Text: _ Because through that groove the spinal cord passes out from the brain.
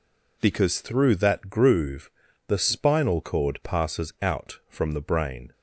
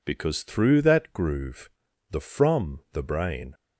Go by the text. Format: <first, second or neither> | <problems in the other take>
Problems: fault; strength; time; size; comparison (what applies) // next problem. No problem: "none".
first | pauses between "groove" and "the"; at 1.6 s; 0.40 s long; slight in the first // skips "spinal cord passes out"; at 2.1 s